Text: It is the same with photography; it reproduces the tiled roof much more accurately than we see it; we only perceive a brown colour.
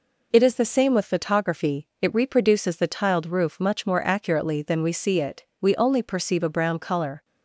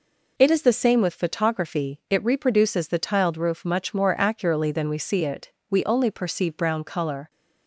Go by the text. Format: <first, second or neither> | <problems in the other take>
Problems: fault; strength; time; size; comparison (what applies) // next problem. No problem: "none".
first | skips "a"; at 6.5 s